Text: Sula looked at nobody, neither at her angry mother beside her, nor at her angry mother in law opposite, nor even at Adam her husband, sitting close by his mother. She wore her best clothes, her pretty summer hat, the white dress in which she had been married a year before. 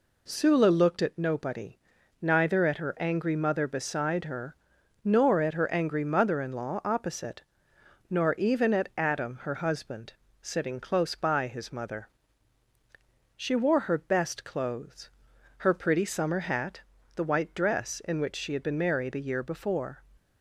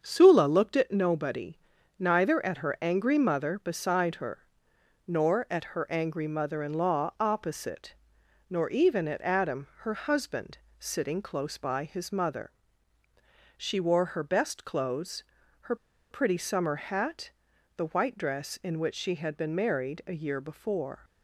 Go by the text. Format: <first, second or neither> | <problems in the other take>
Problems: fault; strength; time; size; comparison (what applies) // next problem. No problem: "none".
first | starts louder than the rest; until 1.0 s; 7 dB // pauses between "her" and "pretty"; slight; at 15.7 s; 0.35 s long